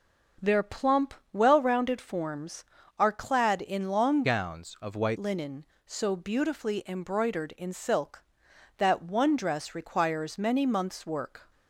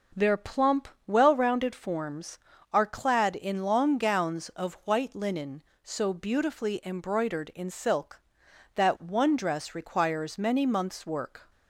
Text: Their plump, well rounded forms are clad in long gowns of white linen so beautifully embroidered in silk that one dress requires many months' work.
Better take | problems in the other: second | starts louder than the rest; until 1.6 s; 6.5 dB // changes voice from "gowns" to "white"; from 4.2 to 5.1 s; 0.9 s long

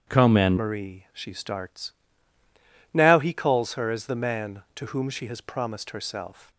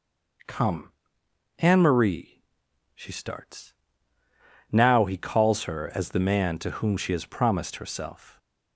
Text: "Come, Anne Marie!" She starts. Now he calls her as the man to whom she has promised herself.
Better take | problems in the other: second | starts louder than the rest; strong; until 1.1 s; 8.5 dB; noticeable in the second // changes voice at "Marie"; from 0.5 s on; 6.0 s long

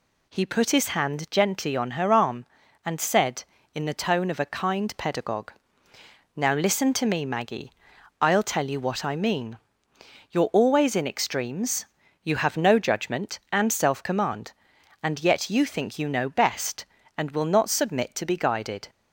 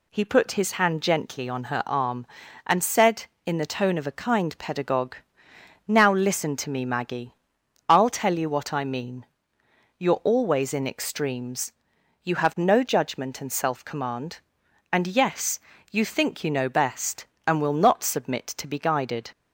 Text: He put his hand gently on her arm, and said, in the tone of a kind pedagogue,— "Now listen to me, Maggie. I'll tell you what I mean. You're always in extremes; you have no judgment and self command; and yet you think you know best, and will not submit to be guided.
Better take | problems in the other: first | says "yes" for "yet"; at 15.0 s

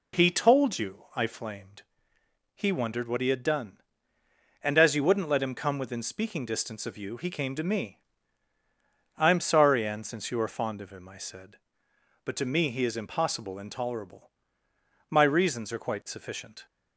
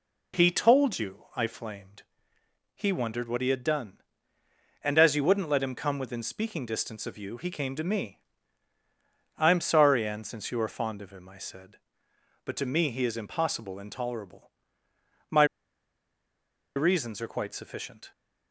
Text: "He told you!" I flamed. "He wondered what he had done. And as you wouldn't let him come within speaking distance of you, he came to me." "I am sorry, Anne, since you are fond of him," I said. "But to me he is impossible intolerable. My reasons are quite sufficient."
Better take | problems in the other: first | pauses between "My" and "reasons"; strong; at 15.4 s; 1.3 s long

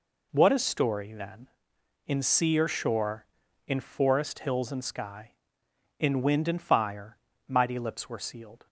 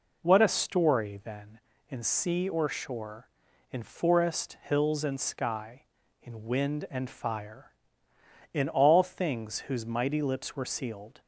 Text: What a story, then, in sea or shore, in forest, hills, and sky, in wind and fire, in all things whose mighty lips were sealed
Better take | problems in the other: second | skips "in all things whose"; at 7.3 s

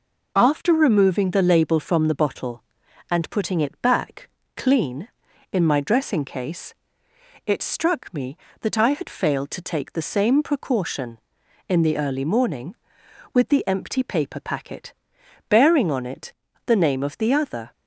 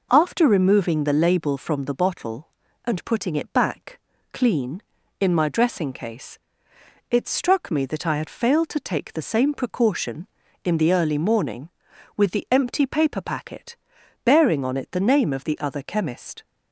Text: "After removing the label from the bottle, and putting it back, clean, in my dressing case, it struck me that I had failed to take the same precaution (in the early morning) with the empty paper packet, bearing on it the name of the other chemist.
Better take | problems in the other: second | pauses between "it" and "the"; slight; at 16.3 s; 0.34 s long // stops before "chemist"; at 17.7 s

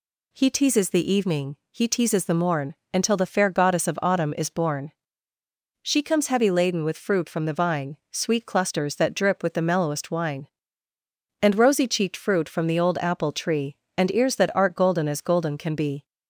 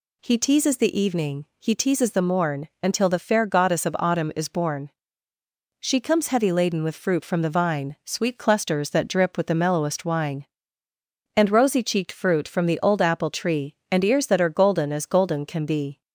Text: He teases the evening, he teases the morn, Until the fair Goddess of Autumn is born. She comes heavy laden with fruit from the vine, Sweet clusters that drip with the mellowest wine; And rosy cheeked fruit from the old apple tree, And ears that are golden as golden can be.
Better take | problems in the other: second | says "art" for "are"; at 14.5 s

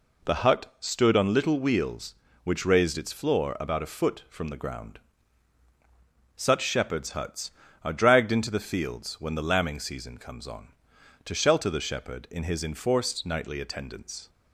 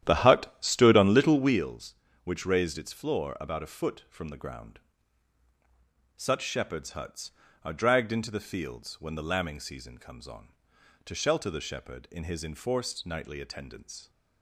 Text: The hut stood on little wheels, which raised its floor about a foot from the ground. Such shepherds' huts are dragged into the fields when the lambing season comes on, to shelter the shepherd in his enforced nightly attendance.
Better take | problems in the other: first | starts louder than the rest; strong; until 1.6 s; 11 dB

